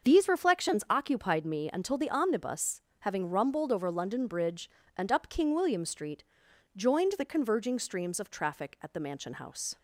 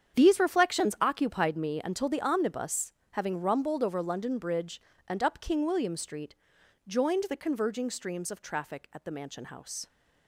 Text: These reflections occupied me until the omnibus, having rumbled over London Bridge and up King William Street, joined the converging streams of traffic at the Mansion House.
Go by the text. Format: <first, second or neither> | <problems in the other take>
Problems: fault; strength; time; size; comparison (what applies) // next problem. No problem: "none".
first | gets quieter; strong; throughout; 14 dB // starts louder than the rest; strong; until 1.2 s; 8.5 dB; also in the first